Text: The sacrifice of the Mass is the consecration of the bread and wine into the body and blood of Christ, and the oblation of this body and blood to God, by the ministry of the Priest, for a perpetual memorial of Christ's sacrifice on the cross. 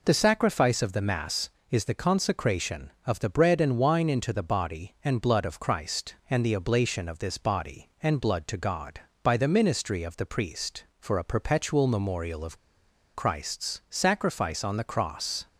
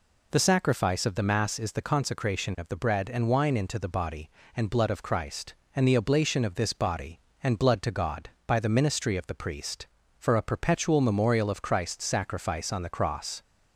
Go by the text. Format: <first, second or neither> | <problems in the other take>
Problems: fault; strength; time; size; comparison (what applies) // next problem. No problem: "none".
second | pauses between "of" and "Christ's"; noticeable; at 12.5 s; 0.57 s long